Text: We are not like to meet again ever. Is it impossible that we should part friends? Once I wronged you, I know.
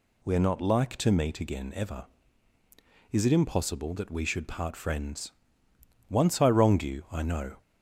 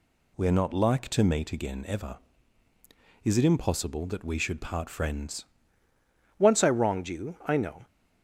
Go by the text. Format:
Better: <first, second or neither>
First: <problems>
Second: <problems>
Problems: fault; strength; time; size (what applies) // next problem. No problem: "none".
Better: first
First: none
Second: changes voice at "Once"; from 6.3 s on; 1.5 s long